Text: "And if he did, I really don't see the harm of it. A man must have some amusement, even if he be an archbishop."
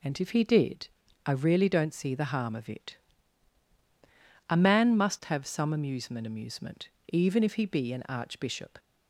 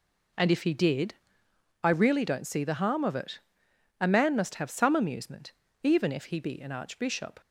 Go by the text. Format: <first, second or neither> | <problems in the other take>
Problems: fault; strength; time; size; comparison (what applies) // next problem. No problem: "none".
second | says "amusement" twice; at 6.2 s